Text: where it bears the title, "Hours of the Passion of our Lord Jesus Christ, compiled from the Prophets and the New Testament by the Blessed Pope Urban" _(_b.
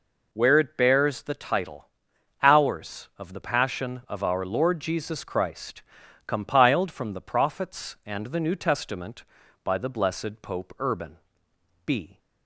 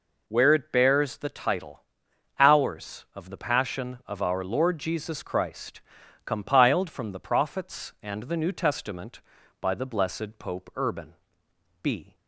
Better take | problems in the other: neither | none

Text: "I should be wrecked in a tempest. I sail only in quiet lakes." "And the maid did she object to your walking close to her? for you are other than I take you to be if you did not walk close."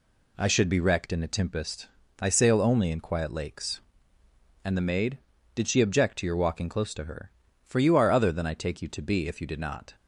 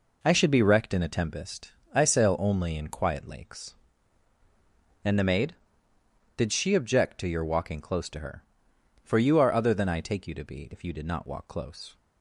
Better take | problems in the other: second | stops before "walk close"; at 9.9 s

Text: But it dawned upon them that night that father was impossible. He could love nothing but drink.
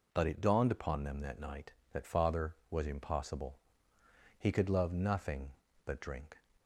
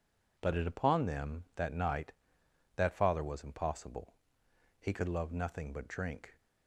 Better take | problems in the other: first | skips "dawned"; at 0.6 s

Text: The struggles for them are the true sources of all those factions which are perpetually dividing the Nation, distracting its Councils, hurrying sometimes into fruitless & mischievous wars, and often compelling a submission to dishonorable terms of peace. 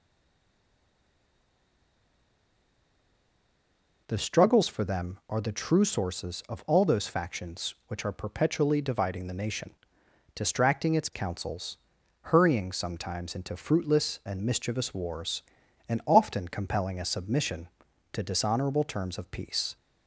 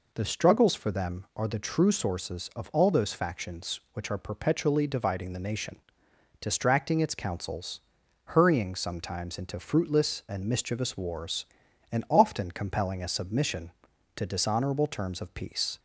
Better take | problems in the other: second | stays silent before the first word; strong; until 4.0 s; 4.0 s long

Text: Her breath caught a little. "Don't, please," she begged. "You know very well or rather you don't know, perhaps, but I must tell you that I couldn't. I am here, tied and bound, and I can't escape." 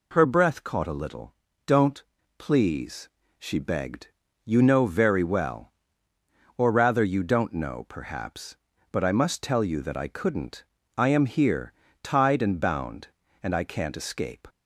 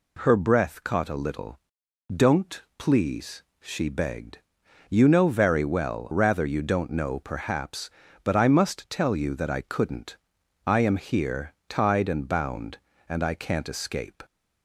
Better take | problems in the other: first | skips "or"; at 6.1 s

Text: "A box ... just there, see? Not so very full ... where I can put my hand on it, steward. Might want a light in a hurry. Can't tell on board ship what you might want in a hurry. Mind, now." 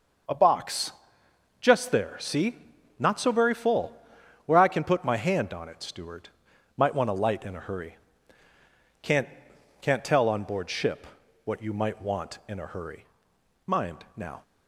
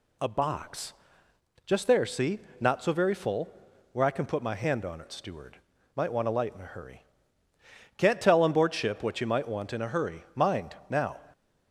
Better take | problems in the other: second | starts louder than the rest; noticeable; until 1.9 s; 6 dB // says "Can't" twice; at 9.8 s // pauses between "ship" and "what"; at 11.0 s; 0.38 s long

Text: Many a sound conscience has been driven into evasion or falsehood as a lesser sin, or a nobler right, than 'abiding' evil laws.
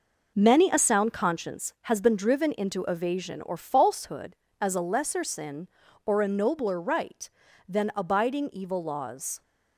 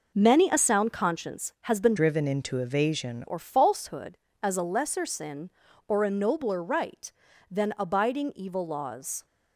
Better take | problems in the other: first | changes voice from "driven" to "evasion"; from 1.9 to 3.2 s; 1.3 s long

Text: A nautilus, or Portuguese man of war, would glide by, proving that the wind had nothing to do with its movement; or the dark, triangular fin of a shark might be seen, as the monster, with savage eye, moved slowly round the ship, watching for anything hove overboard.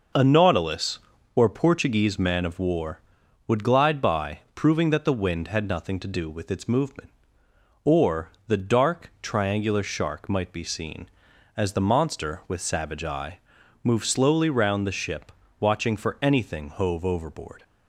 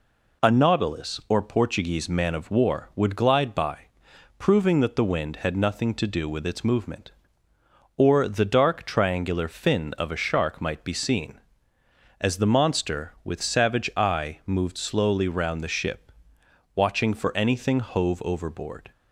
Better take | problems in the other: second | pauses between "or" and "the"; slight; at 8.2 s; 0.18 s long // skips "fin of a"; at 9.8 s

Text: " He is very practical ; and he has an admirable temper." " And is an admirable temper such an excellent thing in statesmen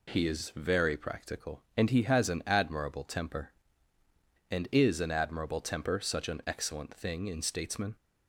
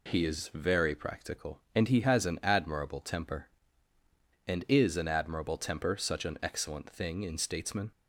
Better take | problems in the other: neither | none

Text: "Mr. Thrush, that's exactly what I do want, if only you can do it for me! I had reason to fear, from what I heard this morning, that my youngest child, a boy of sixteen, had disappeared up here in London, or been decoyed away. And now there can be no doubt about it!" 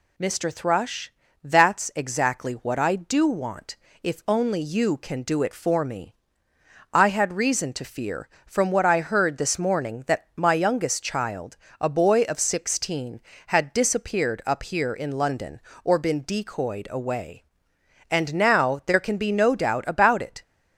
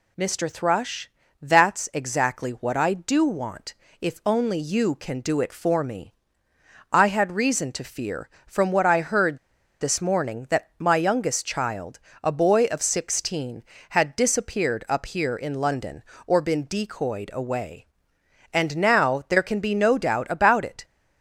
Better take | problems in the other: first | pauses between "heard" and "this"; at 9.3 s; 0.42 s long

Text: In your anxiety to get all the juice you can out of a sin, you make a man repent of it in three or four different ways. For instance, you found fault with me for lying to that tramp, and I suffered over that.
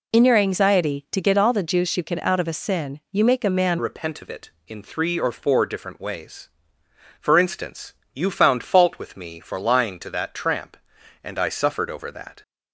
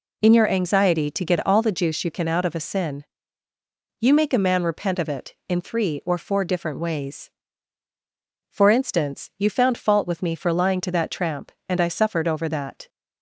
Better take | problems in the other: second | changes voice at "repent"; from 3.7 s on; 8.7 s long

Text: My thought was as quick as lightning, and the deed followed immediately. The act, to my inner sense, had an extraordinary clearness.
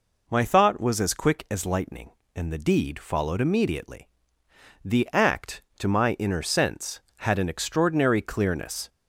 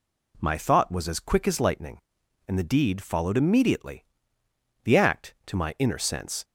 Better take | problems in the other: first | stops before "had an extraordinary clearness"; at 6.4 s

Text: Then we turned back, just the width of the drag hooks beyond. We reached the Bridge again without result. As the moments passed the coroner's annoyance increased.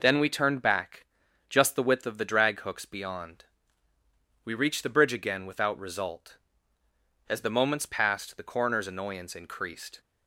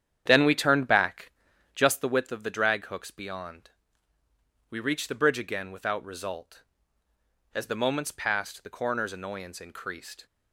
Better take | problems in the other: first | starts louder than the rest; strong; until 1.9 s; 9 dB

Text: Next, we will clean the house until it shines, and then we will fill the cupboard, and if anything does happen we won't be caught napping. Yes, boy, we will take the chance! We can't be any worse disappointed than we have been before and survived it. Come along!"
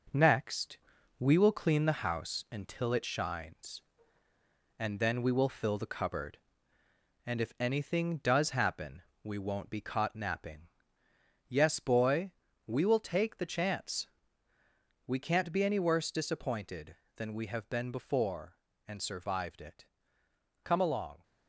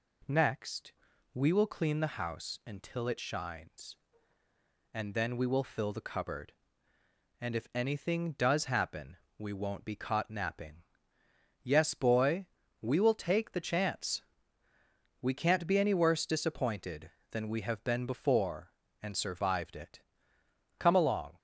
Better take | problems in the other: second | gets quieter; noticeable; throughout; 4.5 dB // pauses between "happen" and "we"; slight; at 9.0 s; 0.22 s long; slight in the second

